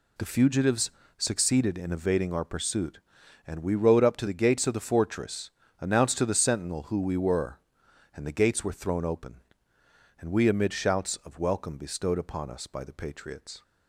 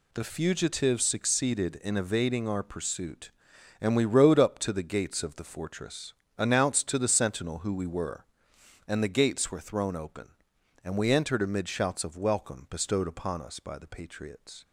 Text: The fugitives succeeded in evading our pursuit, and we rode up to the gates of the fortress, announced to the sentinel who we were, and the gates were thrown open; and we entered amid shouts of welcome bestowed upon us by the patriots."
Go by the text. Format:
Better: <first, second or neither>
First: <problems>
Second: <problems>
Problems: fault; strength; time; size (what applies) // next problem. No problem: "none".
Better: second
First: pauses between "fugitives" and "succeeded"; slight; at 0.8 s; 0.28 s long // skips "entered"; at 10.4 s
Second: none